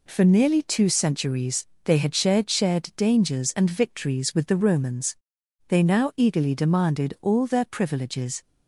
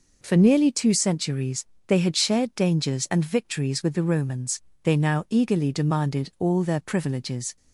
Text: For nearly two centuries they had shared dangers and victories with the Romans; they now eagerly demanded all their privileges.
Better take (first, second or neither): second